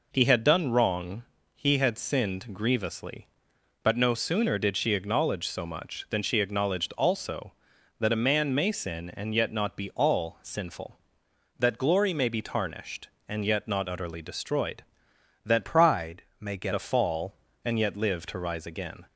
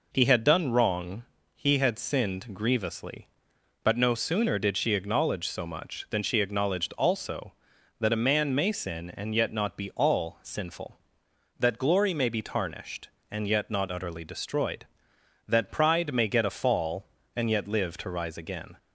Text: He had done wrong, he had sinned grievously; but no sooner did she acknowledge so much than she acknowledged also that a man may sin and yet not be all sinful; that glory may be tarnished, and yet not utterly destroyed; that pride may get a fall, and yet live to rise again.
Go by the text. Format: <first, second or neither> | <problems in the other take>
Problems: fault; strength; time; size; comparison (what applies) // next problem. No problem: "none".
second | changes voice from "pride" to "get"; from 15.6 to 16.7 s; 1.1 s long // pauses between "pride" and "may"; slight; at 16.2 s; 0.16 s long